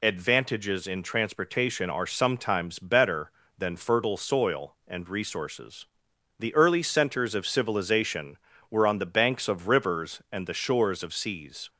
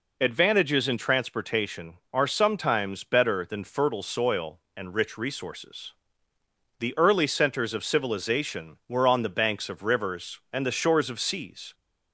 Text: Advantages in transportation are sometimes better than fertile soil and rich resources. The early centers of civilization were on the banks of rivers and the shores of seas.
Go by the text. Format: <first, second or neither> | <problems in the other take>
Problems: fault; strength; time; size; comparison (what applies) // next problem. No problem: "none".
second | skips "rich"; at 5.0 s